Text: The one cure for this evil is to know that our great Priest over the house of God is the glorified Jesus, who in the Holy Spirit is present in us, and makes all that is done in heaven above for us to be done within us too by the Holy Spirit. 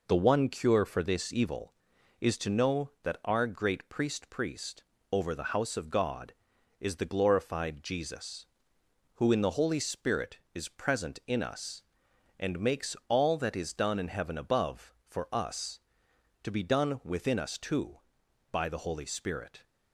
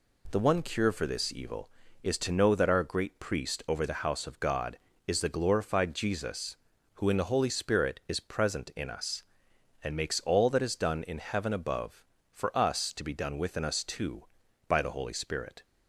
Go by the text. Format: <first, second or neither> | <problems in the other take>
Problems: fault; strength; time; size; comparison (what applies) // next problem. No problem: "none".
second | says "Priest" twice; at 4.3 s